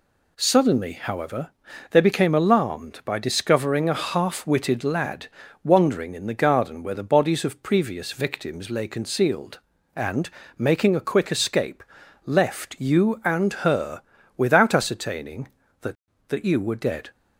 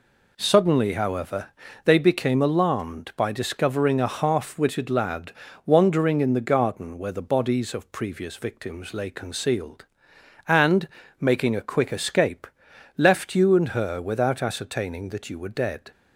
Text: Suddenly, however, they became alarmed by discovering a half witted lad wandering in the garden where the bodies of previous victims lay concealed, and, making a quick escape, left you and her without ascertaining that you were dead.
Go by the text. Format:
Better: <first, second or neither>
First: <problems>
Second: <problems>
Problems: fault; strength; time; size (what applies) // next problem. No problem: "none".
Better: second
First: pauses between "lad" and "wandering"; slight; at 5.2 s; 0.36 s long // pauses between "her" and "without"; slight; at 14.0 s; 0.36 s long // says "that" twice; at 16.2 s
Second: pauses between "lad" and "wandering"; slight; at 5.3 s; 0.34 s long